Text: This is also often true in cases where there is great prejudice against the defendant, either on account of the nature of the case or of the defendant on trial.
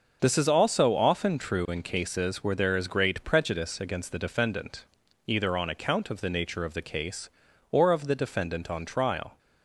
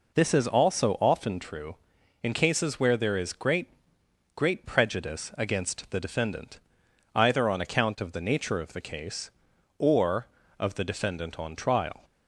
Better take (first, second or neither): first